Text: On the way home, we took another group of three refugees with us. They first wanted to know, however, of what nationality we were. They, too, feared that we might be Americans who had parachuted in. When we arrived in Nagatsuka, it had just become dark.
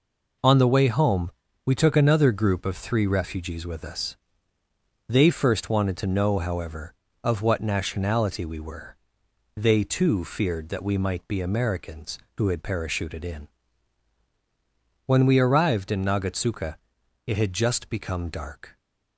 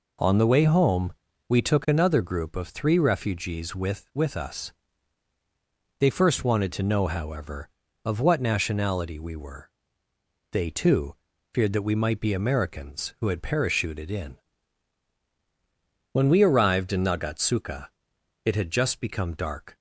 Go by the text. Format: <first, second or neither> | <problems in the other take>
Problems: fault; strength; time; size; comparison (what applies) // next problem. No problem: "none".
first | says "with" twice; at 4.1 s